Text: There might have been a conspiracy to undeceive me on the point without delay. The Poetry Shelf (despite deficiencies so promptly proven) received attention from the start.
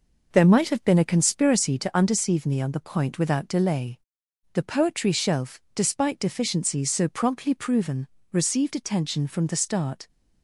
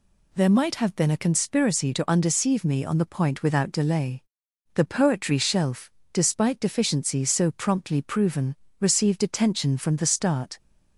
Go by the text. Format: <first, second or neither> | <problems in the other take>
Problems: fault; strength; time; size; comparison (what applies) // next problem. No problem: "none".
second | starts louder than the rest; noticeable; until 1.9 s; 5.5 dB